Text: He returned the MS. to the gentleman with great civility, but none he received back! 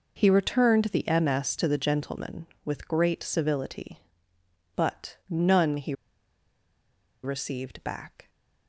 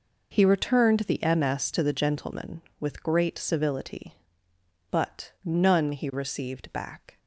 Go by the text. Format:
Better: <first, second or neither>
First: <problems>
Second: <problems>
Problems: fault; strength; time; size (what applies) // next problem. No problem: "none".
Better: second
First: pauses between "he" and "received"; strong; at 5.9 s; 1.3 s long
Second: none